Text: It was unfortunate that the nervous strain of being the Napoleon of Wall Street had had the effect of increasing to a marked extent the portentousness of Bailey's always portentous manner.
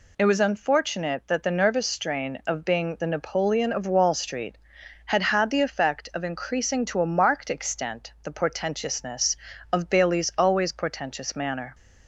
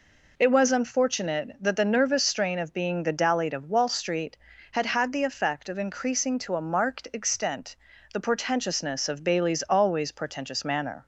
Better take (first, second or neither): first